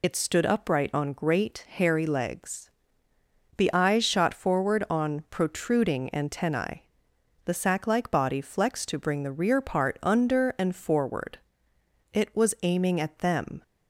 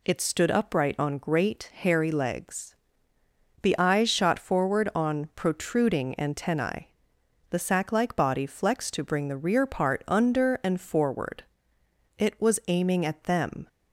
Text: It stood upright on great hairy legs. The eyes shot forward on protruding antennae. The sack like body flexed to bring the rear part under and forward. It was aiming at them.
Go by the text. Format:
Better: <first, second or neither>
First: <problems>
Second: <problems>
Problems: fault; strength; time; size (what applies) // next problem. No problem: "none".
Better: second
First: loses the start of "It"; at 0.0 s; 55 ms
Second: none